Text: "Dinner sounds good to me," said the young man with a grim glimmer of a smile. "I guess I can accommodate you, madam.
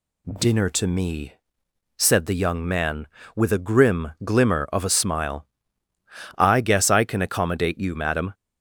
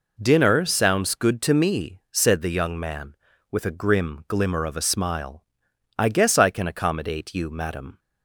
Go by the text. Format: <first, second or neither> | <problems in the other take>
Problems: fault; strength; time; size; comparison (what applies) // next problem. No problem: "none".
second | skips "sounds good"; at 0.6 s